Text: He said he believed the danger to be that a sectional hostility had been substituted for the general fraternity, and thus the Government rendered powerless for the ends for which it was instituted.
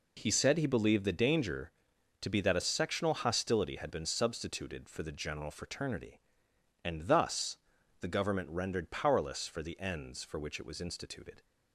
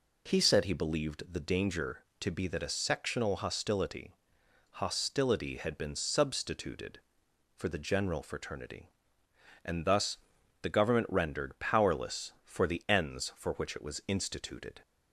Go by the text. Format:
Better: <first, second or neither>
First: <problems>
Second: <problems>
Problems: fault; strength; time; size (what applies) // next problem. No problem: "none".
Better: first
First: pauses between "thus" and "the"; at 7.5 s; 0.42 s long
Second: says "hostility" twice; at 4.8 s // pauses between "thus" and "the"; noticeable; at 10.1 s; 0.46 s long